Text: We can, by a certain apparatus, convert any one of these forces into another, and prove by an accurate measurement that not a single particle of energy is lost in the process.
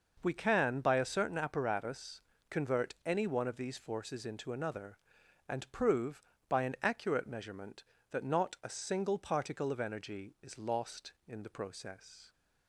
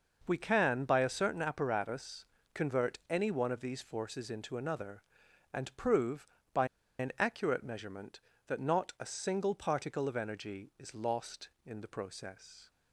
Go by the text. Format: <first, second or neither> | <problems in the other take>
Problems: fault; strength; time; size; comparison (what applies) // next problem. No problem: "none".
first | pauses between "by" and "an"; slight; at 6.6 s; 0.32 s long